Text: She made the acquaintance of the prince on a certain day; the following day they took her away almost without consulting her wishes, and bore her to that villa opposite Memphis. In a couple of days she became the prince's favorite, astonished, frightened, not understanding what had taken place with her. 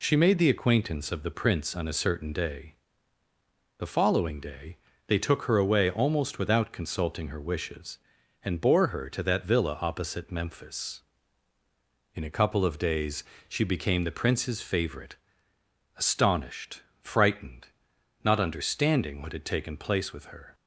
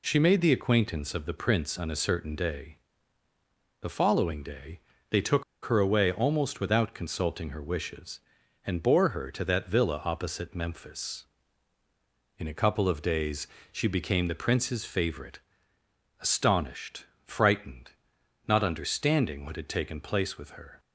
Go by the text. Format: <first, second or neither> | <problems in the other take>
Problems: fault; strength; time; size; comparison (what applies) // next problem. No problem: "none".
first | pauses between "day" and "they"; slight; at 4.8 s; 0.28 s long; slight in the first // pauses between "took" and "her"; slight; at 5.4 s; 0.21 s long // pauses between "days" and "she"; slight; at 13.4 s; 0.22 s long; slight in the first